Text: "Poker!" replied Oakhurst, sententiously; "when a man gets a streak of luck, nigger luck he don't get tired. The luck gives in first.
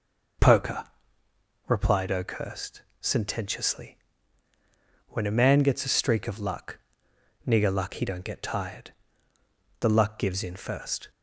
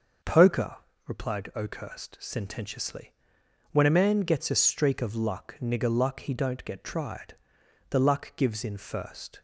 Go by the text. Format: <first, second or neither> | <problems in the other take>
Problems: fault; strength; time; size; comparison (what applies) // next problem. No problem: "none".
first | starts louder than the rest; noticeable; until 1.6 s; 6 dB // says "tried" for "tired"; at 6.8 s